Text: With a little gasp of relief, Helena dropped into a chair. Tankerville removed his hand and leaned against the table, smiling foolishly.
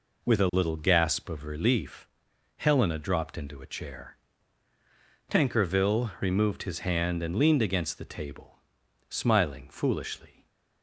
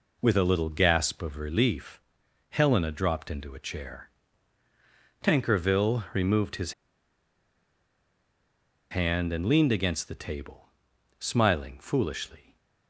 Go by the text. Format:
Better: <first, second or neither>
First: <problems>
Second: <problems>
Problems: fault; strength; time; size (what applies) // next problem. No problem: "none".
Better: first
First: none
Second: pauses between "his" and "hand"; strong; at 6.7 s; 2.1 s long